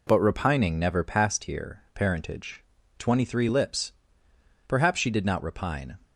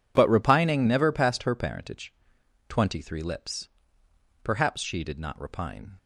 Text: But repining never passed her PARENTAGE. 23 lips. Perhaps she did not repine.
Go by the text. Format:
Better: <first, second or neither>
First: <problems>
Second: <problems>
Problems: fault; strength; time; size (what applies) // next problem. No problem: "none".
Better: second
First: says "here" for "her"; at 1.4 s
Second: none